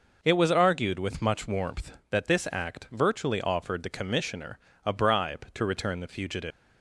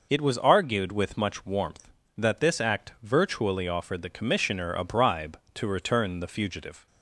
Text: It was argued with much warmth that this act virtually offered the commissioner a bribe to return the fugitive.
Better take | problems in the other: second | pauses between "commissioner" and "a"; slight; at 4.5 s; 0.26 s long // leaves "fugitive" unfinished; at 6.5 s; 165 ms

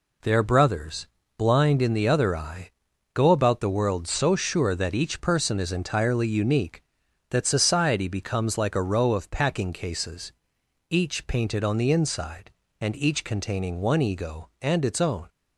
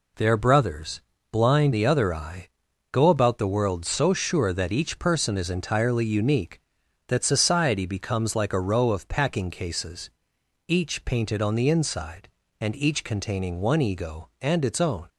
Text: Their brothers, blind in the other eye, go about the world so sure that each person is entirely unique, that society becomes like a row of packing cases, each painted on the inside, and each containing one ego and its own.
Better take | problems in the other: first | skips "in"; at 1.7 s

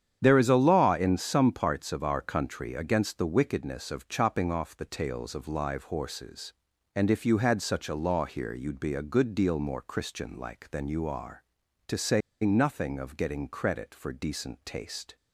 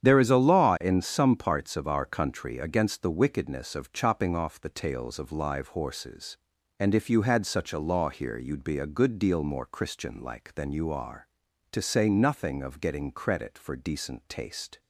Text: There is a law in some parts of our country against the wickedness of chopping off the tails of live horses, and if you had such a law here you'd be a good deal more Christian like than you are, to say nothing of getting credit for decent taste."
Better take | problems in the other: second | starts louder than the rest; strong; until 1.2 s; 9 dB; strong in the second // pauses between "say" and "nothing"; slight; at 12.2 s; 0.23 s long

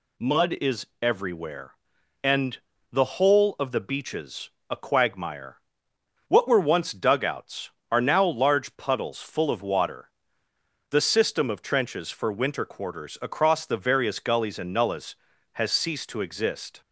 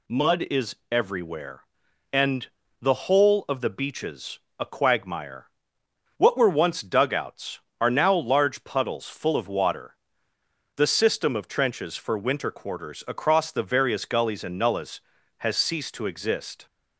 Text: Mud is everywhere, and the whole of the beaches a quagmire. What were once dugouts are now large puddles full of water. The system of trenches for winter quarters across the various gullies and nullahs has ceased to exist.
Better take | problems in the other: neither | pauses between "is" and "everywhere"; slight; the same in both // pauses between "and" and "the"; slight; the same in both // pauses between "beaches" and "a"; slight; the same in both

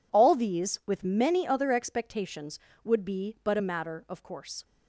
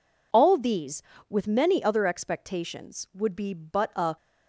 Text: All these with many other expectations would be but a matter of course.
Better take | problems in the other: first | stops before "matter of course"; at 4.1 s

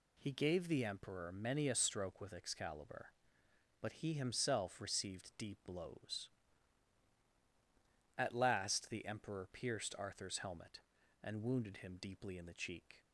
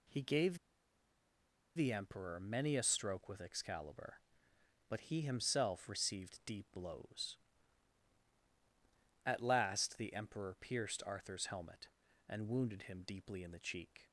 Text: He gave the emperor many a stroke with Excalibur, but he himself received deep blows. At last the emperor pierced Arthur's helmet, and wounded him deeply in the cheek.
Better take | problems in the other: first | pauses between "gave" and "the"; at 0.5 s; 1.1 s long

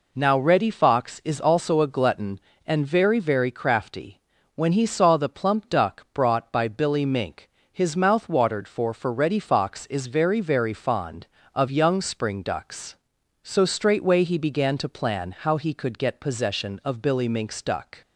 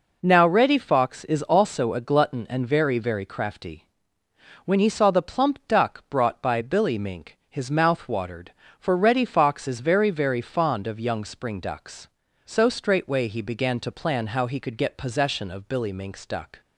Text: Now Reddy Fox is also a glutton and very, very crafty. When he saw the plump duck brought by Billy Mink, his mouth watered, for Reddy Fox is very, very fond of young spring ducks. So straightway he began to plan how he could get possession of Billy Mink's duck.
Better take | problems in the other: second | says "for" twice; at 8.9 s

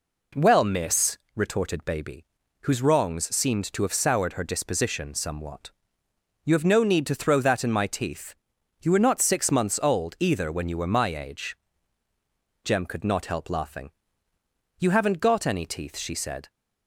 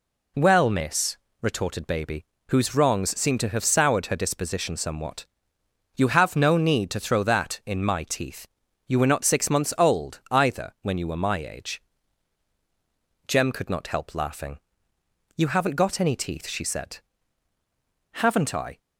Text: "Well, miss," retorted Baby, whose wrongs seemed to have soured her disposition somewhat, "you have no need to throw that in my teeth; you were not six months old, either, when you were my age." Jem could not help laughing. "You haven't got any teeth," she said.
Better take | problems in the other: first | goes on to say "Haven't I"; noticeable; from 18.1 s on; 0.66 s long

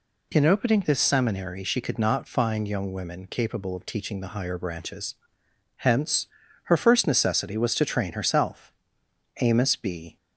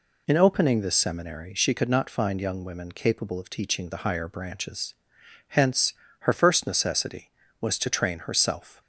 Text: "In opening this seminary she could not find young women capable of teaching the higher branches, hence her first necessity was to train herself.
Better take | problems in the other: second | pauses between "hence" and "her"; at 6.2 s; 0.38 s long; slight in the second // goes on to say "Amos B"; noticeable; from 9.4 s on; 0.76 s long

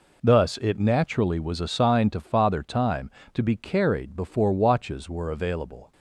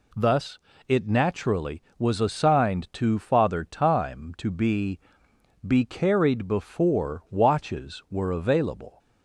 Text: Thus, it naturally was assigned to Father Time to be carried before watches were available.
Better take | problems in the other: first | says "be" twice; at 5.6 s

